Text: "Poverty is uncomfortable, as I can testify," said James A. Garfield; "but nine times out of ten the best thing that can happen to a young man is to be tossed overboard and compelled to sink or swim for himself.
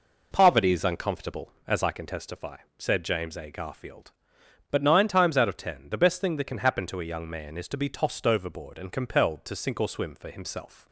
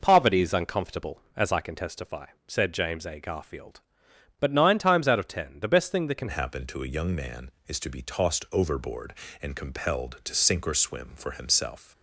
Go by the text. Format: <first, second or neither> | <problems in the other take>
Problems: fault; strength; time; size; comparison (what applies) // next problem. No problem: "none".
first | changes voice at "happen"; from 6.2 s on; 5.7 s long